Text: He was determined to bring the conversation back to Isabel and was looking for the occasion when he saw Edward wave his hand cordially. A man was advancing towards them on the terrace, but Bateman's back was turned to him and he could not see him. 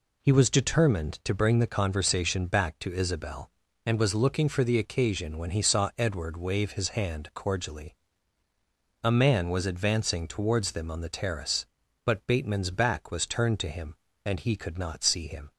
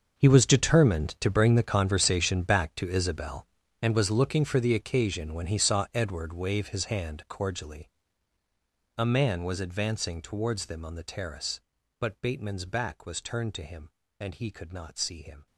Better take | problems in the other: first | gets quieter; strong; throughout; 16.5 dB

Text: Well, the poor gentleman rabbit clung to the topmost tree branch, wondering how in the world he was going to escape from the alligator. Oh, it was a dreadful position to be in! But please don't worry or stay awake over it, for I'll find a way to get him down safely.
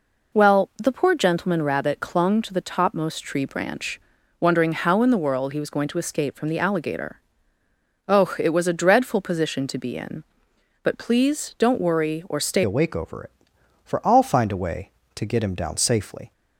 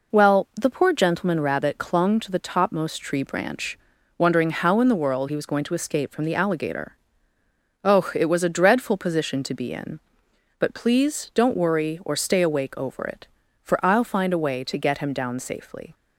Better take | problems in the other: second | changes voice at "awake"; from 12.6 s on; 3.7 s long

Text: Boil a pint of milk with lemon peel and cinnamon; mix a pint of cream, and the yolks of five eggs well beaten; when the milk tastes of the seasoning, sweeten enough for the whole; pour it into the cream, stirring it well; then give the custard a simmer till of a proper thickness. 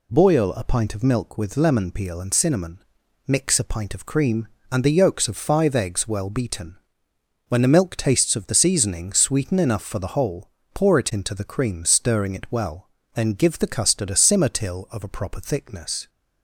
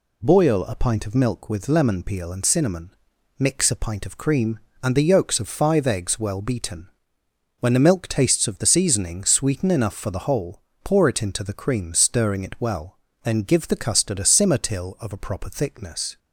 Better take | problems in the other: neither | none

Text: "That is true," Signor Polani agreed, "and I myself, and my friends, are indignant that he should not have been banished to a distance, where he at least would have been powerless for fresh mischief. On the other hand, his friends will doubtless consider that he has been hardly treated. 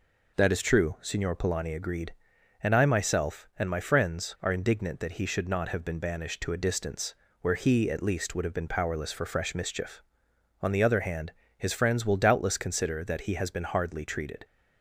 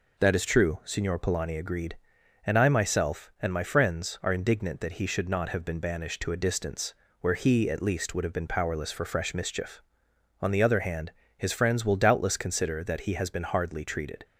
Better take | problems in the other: neither | none

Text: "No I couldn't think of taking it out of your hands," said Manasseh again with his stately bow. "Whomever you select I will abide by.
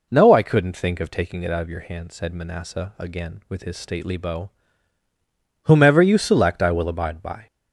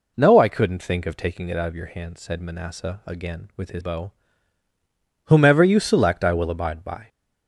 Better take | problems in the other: first | skips "stately"; at 3.8 s

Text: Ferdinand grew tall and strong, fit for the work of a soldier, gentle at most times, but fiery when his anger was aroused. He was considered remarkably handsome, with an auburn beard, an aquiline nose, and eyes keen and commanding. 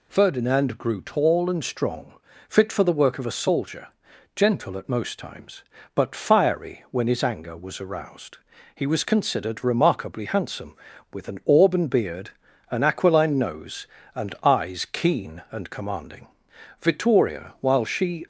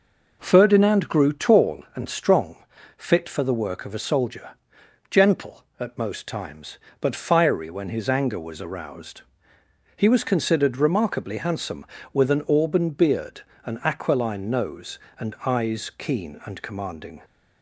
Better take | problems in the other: second | goes on to say "Vittoria while she"; from 16.7 s on; 1.4 s long

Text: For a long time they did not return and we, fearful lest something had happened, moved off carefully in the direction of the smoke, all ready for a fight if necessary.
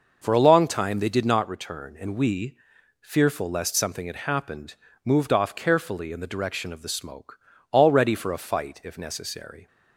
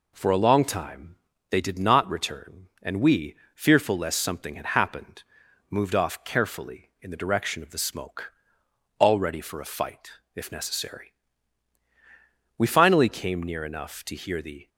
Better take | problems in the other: first | pauses between "time" and "they"; slight; at 1.1 s; 0.34 s long // pauses between "fight" and "if"; slight; at 10.1 s; 0.22 s long // goes on to say "We finally came near enough to hear the"; strong; from 12.5 s on; 2.1 s long

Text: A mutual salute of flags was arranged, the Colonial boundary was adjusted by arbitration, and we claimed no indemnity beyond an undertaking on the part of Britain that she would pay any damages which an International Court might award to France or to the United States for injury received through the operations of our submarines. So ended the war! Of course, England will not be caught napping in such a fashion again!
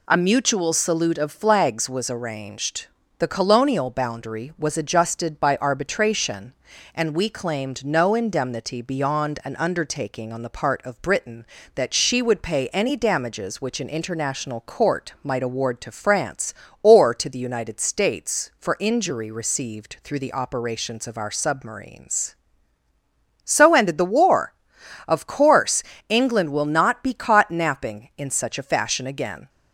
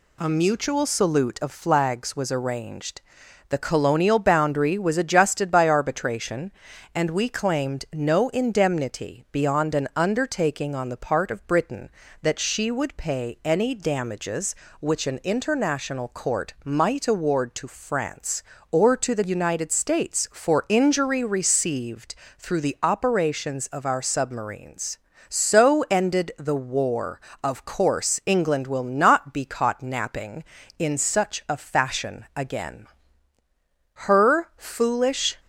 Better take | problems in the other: first | pauses between "received" and "through"; slight; at 22.1 s; 0.24 s long // goes on to say "Her foolish"; from 34.0 s on; 1.3 s long

